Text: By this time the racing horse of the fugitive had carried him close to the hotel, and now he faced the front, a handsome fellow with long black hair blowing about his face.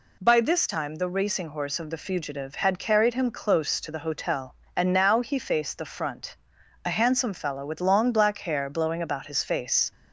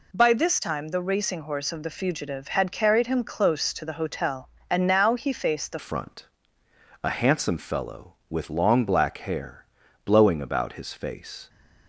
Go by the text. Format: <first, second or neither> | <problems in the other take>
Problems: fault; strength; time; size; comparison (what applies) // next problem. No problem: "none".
first | changes voice at "front"; from 5.7 s on; 5.7 s long // pauses between "hair" and "blowing"; at 9.6 s; 0.40 s long